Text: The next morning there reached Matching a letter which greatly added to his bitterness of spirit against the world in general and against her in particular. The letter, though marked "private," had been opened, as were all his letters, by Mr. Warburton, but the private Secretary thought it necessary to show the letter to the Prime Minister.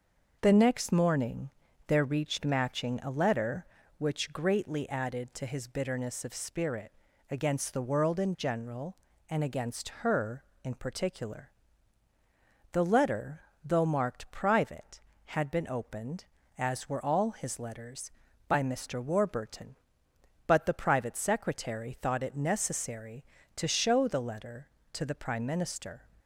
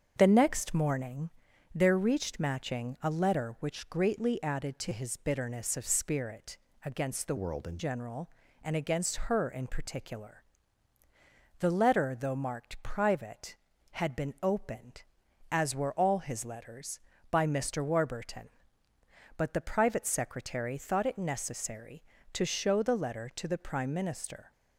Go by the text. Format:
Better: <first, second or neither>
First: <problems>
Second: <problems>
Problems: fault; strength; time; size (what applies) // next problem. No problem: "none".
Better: first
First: starts louder than the rest; until 1.4 s; 6 dB // pauses between "morning" and "there"; at 1.5 s; 0.38 s long // pauses between "spirit" and "against"; slight; at 6.9 s; 0.36 s long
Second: starts louder than the rest; strong; until 1.1 s; 7.5 dB // pauses between "morning" and "there"; noticeable; at 1.2 s; 0.46 s long // pauses between "spirit" and "against"; slight; at 6.5 s; 0.26 s long // changes voice from "world" to "in"; from 7.3 to 7.7 s; 0.4 s long